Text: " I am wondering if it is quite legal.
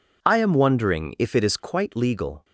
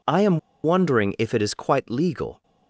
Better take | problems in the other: first | pauses between "am" and "wondering"; slight; at 0.3 s; 0.25 s long

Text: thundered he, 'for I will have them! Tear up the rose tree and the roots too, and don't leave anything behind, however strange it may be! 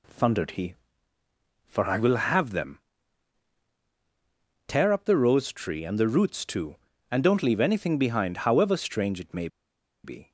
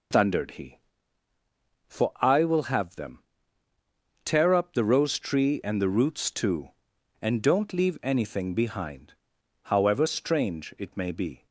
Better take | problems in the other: second | pauses between "may" and "be"; noticeable; at 9.4 s; 0.57 s long

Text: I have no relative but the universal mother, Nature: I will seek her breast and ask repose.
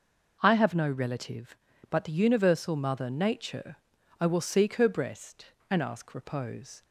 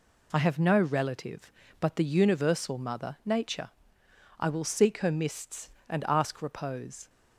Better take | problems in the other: first | says "mists" for "breast"; at 5.1 s

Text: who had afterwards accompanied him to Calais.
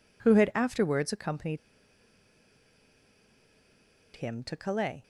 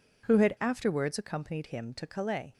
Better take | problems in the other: second | pauses between "accompanied" and "him"; strong; at 1.5 s; 2.5 s long

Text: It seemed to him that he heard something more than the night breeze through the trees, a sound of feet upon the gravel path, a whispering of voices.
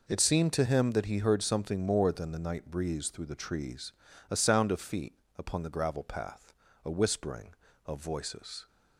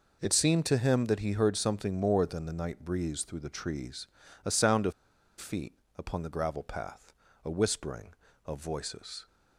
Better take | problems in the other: first | pauses between "of" and "feet"; noticeable; at 4.9 s; 0.47 s long // pauses between "feet" and "upon"; slight; at 5.7 s; 0.22 s long; slight in the first

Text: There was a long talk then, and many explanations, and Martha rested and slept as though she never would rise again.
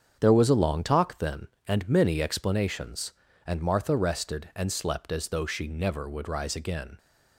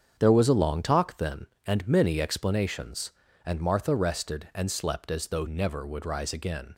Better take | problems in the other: first | starts louder than the rest; strong; until 1.2 s; 8 dB; strong in the first // skips "she"; at 5.4 s

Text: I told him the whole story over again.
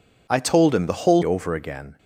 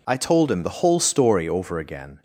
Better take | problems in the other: second | skips "story"; at 1.2 s

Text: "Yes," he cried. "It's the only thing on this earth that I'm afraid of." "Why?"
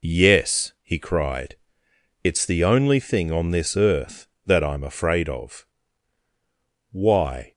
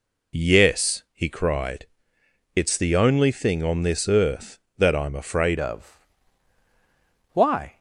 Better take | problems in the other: first | changes voice at "of"; from 5.5 s on; 2.2 s long

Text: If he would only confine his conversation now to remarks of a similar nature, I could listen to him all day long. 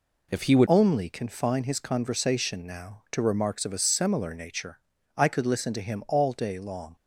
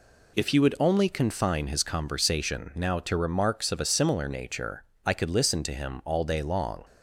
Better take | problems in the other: second | changes voice at "only"; from 0.6 s on; 6.3 s long

